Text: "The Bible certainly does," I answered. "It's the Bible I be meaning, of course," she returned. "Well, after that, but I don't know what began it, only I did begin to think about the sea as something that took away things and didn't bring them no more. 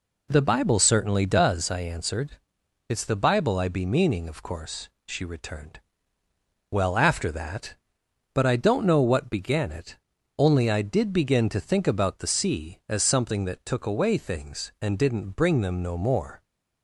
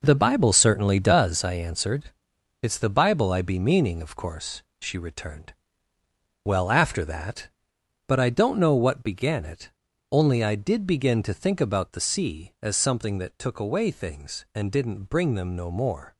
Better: first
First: none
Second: gets quieter; strong; throughout; 9 dB

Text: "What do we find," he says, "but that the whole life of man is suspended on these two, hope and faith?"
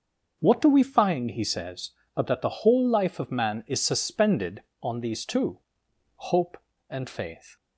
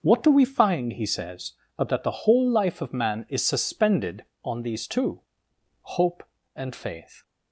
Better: neither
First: starts louder than the rest; noticeable; until 1.4 s; 6 dB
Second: starts louder than the rest; until 1.0 s; 6 dB

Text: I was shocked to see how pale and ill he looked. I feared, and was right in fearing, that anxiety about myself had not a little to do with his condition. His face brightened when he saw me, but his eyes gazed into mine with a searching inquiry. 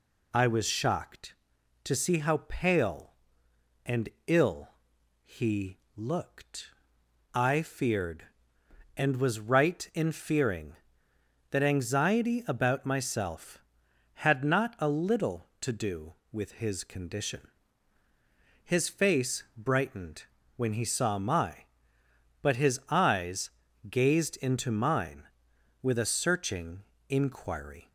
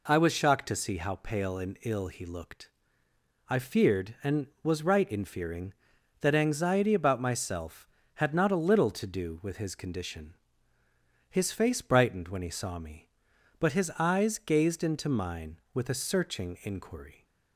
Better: second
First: pauses between "and" and "ill"; slight; at 4.0 s; 0.20 s long // pauses between "ill" and "he"; noticeable; at 4.6 s; 0.56 s long // pauses between "he" and "looked"; slight; at 5.7 s; 0.20 s long // pauses between "brightened" and "when"; slight; at 20.2 s; 0.32 s long // says "my" for "me"; at 21.1 s // pauses between "eyes" and "gazed"; at 23.4 s; 0.40 s long // pauses between "searching" and "inquiry"; slight; at 26.8 s; 0.26 s long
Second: none

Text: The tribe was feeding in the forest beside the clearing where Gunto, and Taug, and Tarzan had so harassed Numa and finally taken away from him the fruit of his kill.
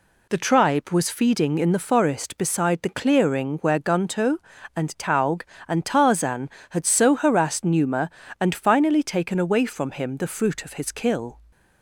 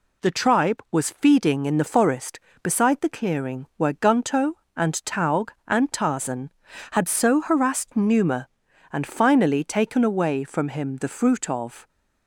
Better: first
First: none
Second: stops before "his kill"; at 11.8 s

